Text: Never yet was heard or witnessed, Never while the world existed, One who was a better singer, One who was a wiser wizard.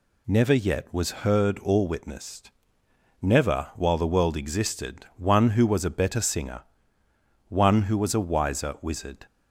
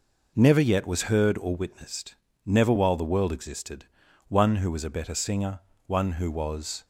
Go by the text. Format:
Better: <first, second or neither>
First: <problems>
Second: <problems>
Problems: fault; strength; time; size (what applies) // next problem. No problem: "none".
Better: first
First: none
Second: stops before "a wiser wizard"; at 6.8 s